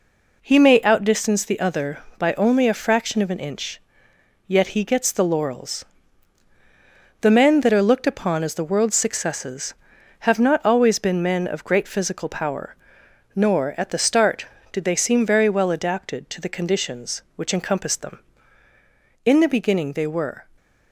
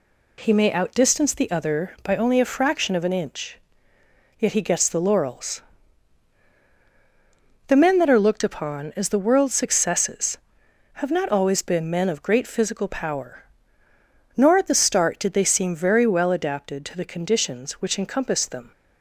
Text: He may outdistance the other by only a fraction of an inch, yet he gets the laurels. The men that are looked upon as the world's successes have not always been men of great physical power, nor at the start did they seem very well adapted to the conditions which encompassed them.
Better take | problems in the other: second | goes on to say "In the beginning they were"; noticeable; from 19.2 s on; 1.2 s long

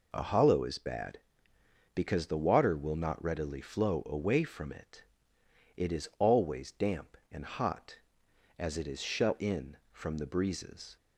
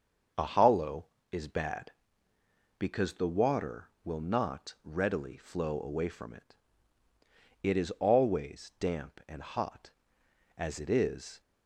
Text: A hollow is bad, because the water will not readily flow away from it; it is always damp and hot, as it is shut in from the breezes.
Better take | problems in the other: first | starts louder than the rest; until 1.6 s; 6.5 dB // stops before "shut in from the breezes"; at 11.4 s

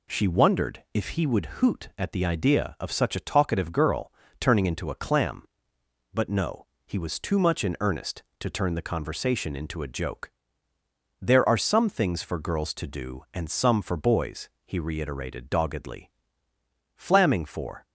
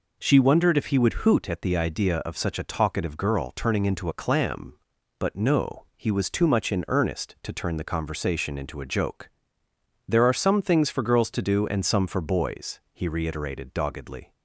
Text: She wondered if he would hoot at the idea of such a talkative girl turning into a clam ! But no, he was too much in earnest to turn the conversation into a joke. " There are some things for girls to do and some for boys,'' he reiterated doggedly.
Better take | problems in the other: second | pauses between "girl" and "turning"; slight; at 4.1 s; 0.30 s long // goes on to say "flamming for"; noticeable; from 16.9 s on; 0.88 s long

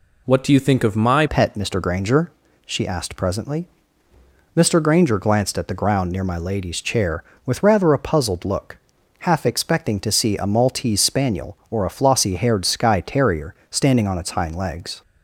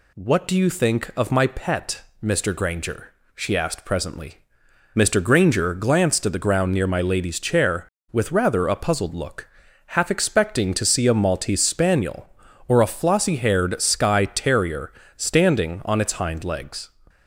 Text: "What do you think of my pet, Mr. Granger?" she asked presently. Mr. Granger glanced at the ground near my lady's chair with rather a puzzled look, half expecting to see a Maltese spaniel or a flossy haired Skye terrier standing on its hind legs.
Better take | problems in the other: second | changes voice at "pet"; from 1.2 s on; 13.8 s long // pauses between "terrier" and "standing"; slight; at 13.5 s; 0.16 s long; slight in the second

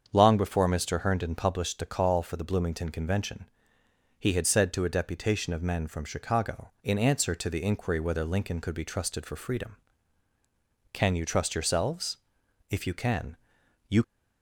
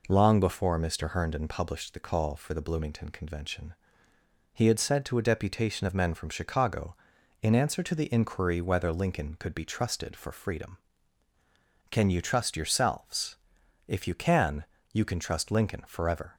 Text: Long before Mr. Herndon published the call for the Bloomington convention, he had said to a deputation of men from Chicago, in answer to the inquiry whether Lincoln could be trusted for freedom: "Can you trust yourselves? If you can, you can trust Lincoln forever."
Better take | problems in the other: second | starts louder than the rest; strong; until 1.1 s; 7 dB // stops before "can trust Lincoln forever"; at 14.0 s

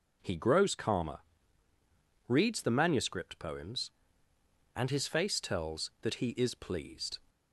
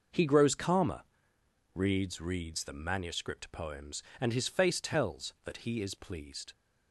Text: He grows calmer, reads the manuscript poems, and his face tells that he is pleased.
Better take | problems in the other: first | says "reads" twice; at 2.1 s

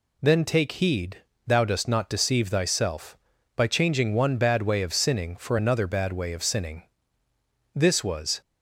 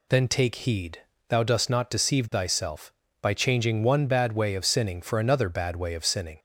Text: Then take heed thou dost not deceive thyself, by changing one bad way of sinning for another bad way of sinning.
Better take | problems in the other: second | pauses between "heed" and "thou"; slight; at 1.1 s; 0.28 s long; slight in the second // goes on to say "This was"; noticeable; from 7.7 s on; 0.66 s long

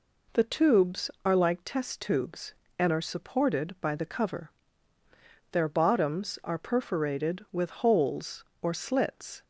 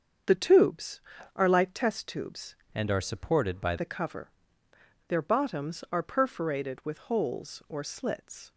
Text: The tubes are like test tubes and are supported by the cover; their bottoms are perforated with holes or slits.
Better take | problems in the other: first | starts louder than the rest; strong; until 1.6 s; 7.5 dB // changes voice from "and" to "by"; from 2.7 to 3.7 s; 1.0 s long

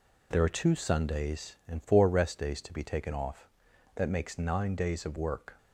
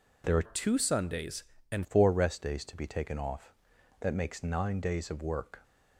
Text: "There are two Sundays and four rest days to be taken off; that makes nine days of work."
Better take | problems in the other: first | changes voice from "two" to "and"; from 0.4 to 1.8 s; 1.4 s long

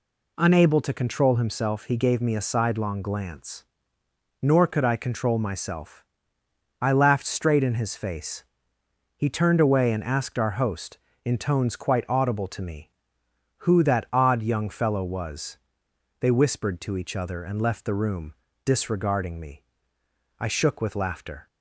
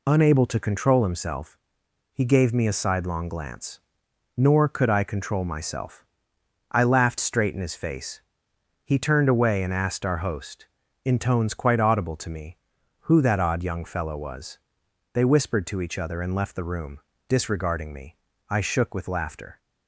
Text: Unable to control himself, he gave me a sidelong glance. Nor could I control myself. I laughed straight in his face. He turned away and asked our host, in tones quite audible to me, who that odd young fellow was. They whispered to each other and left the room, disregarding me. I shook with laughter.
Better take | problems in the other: neither | none

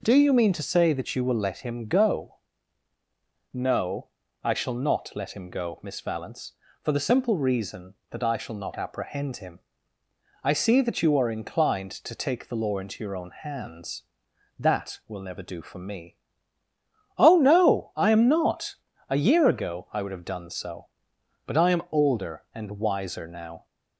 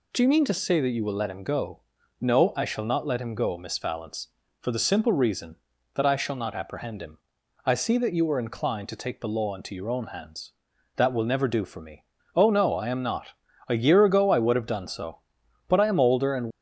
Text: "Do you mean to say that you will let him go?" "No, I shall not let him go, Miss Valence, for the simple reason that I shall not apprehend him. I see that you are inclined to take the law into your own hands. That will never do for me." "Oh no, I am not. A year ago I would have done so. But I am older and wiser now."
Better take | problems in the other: first | stops before "wiser now"; at 16.4 s

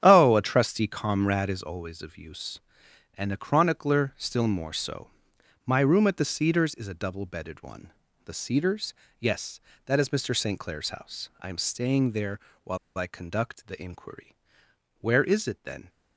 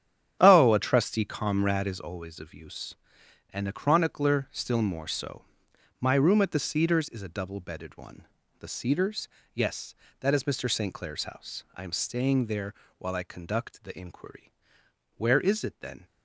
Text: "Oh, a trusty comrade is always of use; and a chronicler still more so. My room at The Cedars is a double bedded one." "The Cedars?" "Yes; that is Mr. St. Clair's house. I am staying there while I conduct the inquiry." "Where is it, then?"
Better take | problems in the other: second | starts louder than the rest; strong; until 1.0 s; 10 dB; strong in the second // pauses between "there" and "while"; slight; at 12.3 s; 0.24 s long; slight in the second // pauses between "while" and "I"; slight; at 12.7 s; 0.21 s long

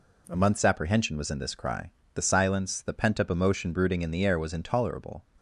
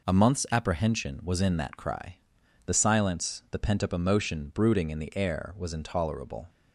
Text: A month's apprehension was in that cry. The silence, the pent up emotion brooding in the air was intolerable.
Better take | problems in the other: second | says "this" for "that"; at 1.3 s

